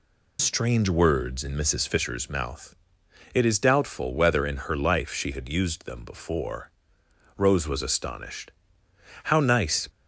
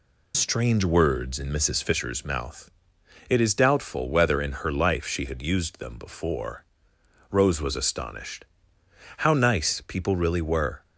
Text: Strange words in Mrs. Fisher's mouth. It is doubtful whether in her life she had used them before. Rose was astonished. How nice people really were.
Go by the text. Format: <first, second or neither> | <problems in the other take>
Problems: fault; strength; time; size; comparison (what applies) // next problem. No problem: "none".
second | stops before "people really were"; at 9.8 s